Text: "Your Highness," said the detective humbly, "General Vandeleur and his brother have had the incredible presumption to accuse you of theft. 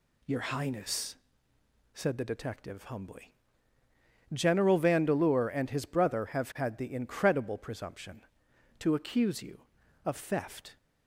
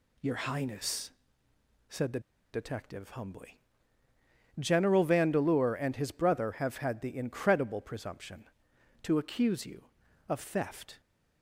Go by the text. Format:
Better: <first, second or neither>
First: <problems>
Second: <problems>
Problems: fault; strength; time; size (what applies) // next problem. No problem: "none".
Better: first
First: none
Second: pauses between "the" and "detective"; slight; at 2.1 s; 0.33 s long